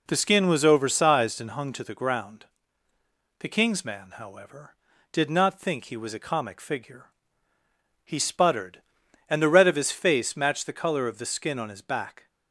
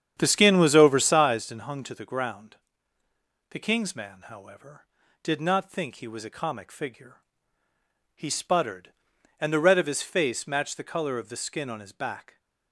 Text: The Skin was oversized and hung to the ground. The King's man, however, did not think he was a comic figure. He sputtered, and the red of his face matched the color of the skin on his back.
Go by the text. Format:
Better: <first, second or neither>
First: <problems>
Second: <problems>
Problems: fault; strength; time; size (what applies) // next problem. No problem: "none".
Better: first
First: none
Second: starts louder than the rest; strong; until 1.3 s; 8.5 dB